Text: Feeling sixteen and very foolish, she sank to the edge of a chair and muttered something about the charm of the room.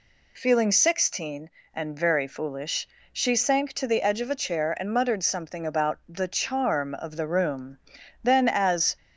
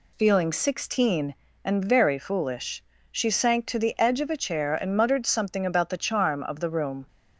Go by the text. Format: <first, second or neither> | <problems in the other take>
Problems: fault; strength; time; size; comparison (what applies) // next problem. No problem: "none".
second | goes on to say "Then as"; noticeable; from 8.2 s on; 0.74 s long